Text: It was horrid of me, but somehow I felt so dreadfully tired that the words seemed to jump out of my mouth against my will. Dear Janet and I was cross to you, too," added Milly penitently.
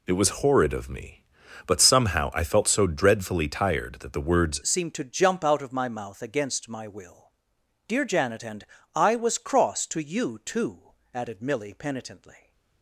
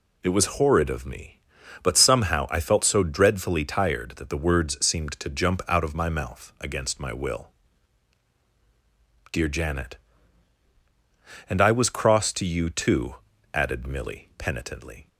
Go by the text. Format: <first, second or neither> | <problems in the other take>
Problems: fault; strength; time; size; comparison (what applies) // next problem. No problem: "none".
second | changes voice at "seemed"; from 4.6 s on; 7.9 s long // pauses between "and" and "I"; slight; at 8.6 s; 0.30 s long